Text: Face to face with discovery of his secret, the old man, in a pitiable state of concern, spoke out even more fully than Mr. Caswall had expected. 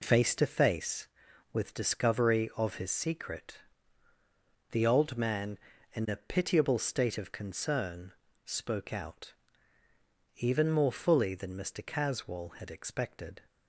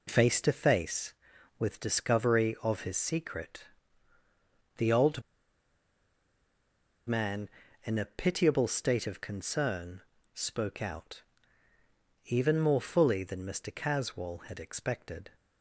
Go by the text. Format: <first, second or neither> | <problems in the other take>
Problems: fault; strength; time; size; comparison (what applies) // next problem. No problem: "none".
first | pauses between "old" and "man"; strong; at 5.2 s; 1.8 s long // pauses between "out" and "even"; at 11.2 s; 1.0 s long; also in the first